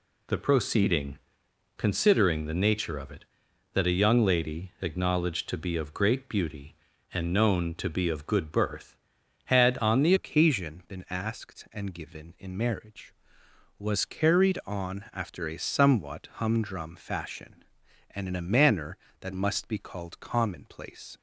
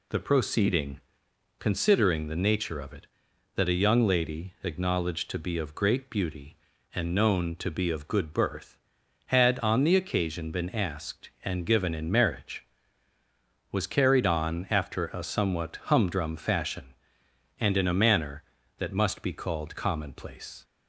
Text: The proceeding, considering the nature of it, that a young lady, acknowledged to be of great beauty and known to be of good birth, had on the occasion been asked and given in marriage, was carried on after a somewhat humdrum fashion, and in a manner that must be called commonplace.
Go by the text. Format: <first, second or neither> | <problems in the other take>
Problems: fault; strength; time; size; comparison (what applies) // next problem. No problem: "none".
second | changes voice at "occasion"; from 10.1 s on; 11.0 s long